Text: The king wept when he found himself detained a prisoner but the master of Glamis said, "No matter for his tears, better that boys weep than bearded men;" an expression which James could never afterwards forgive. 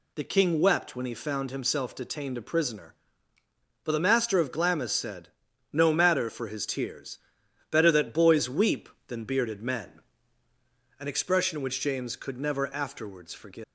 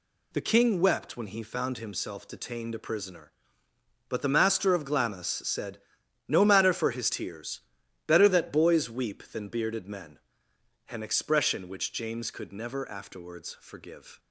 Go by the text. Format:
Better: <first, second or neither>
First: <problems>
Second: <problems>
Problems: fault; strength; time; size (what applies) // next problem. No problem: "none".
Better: second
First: leaves "forgive" unfinished; at 13.6 s; 235 ms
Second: none